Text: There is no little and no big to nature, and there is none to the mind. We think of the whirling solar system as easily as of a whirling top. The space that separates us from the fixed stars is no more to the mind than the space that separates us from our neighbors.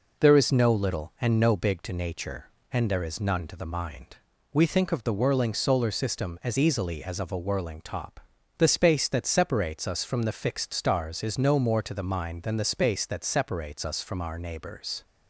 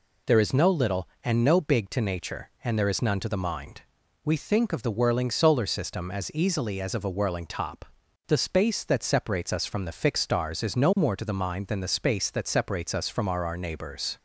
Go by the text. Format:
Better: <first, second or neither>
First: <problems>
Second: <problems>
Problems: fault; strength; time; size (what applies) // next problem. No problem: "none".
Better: first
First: none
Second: says "our" twice; at 13.4 s